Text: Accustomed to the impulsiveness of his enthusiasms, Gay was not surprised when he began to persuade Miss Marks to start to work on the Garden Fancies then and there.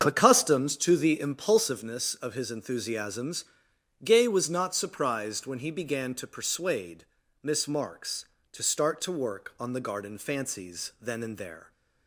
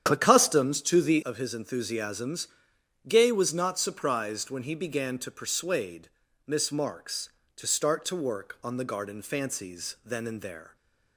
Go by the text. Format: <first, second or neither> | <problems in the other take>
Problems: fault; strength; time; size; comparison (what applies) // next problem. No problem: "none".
first | starts louder than the rest; strong; until 1.0 s; 9 dB; also in the first // skips "impulsiveness"; at 1.2 s // pauses between "persuade" and "Miss"; at 6.0 s; 0.38 s long; also in the first